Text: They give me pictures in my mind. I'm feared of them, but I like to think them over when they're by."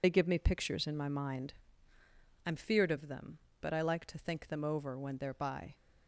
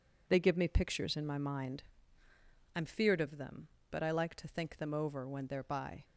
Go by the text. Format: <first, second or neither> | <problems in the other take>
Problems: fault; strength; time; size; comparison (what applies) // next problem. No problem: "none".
second | loses the start of "They"; at 0.0 s; 50 ms